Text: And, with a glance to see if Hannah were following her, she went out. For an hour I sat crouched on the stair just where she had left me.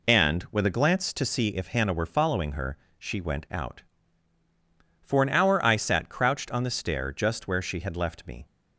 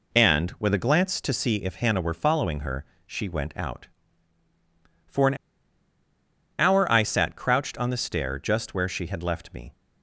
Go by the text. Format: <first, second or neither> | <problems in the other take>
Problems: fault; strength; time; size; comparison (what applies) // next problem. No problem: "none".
first | pauses between "an" and "hour"; at 5.3 s; 1.2 s long